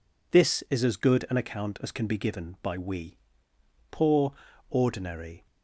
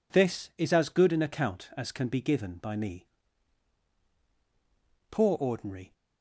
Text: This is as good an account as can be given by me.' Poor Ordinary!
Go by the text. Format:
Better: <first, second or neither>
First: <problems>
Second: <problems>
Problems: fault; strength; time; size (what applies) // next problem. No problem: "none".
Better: second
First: says "we" for "me"; at 2.7 s // pauses between "Poor" and "Ordinary"; slight; at 4.3 s; 0.34 s long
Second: none